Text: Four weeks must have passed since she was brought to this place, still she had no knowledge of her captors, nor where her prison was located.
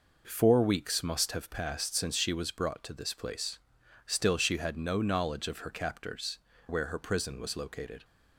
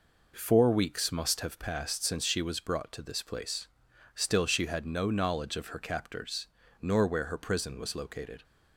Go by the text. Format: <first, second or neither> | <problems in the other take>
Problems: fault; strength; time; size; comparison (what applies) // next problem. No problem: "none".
second | skips "nor"; at 6.5 s